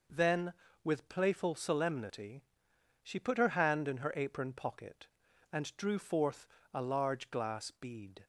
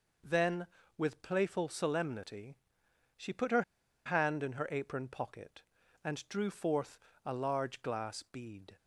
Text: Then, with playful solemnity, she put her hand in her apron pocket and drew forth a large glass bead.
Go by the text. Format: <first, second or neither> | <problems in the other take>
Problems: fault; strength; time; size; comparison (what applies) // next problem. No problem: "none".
first | pauses between "her" and "hand"; at 3.6 s; 0.43 s long // pauses between "forth" and "a"; slight; at 6.9 s; 0.26 s long; slight in the first